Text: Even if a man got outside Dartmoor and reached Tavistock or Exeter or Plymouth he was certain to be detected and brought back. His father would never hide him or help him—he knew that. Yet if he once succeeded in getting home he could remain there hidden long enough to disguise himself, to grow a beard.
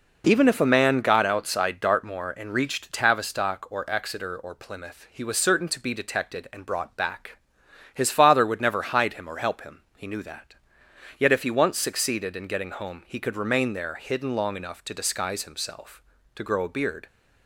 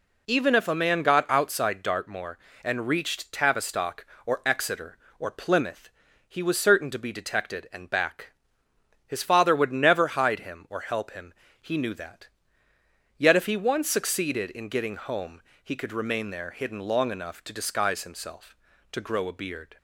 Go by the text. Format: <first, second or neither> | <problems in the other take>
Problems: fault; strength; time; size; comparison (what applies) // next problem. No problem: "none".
first | pauses between "Plymouth" and "he"; at 5.8 s; 0.38 s long // skips "brought"; at 7.8 s // pauses between "home" and "he"; slight; at 15.4 s; 0.22 s long